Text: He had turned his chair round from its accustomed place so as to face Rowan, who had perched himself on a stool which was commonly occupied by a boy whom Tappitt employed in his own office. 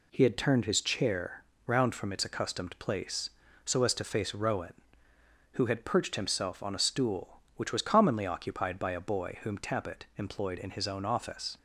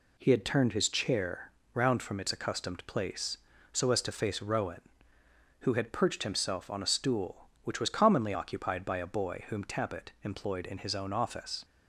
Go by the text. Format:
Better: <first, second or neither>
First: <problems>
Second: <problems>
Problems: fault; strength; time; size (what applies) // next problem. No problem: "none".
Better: neither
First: pauses between "chair" and "round"; slight; at 1.4 s; 0.22 s long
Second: pauses between "chair" and "round"; slight; at 1.5 s; 0.22 s long